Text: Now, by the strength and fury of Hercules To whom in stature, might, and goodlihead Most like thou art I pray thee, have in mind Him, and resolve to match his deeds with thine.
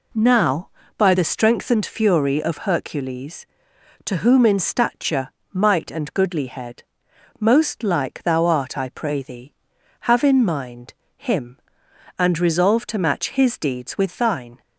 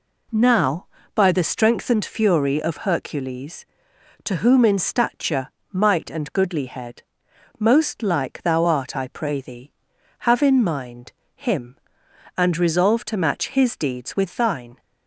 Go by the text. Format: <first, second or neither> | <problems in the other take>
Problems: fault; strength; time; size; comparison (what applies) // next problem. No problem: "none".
neither | pauses between "goodlihead" and "Most"; noticeable; the same in both // pauses between "mind" and "Him"; slight; the same in both